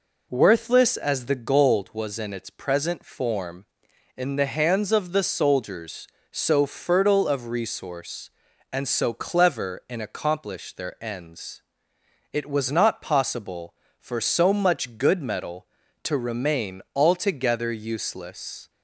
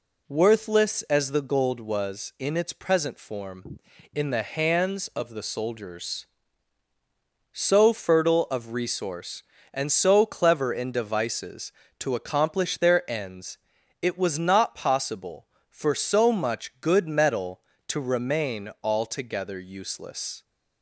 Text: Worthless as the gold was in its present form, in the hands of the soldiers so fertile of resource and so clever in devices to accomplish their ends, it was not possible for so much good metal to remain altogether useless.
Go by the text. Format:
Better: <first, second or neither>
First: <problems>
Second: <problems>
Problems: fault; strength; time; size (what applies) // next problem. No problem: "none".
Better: second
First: skips "devices to"; at 9.9 s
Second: none